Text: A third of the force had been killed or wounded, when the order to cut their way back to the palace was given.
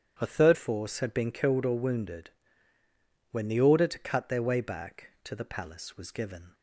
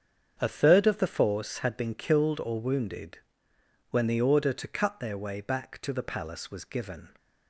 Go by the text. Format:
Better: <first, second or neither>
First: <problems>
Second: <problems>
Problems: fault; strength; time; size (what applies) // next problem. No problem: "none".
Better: second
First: starts louder than the rest; strong; until 1.1 s; 9.5 dB // skips "of the"; at 0.5 s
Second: starts louder than the rest; strong; until 1.3 s; 7.5 dB